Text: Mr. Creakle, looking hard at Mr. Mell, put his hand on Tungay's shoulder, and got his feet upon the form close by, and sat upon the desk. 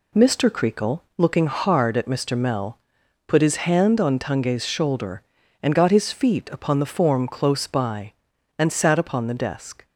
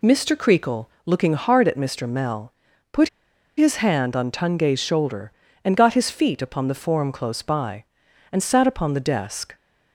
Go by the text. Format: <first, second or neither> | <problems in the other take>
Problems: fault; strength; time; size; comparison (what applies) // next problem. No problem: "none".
first | pauses between "put" and "his"; noticeable; at 3.0 s; 0.48 s long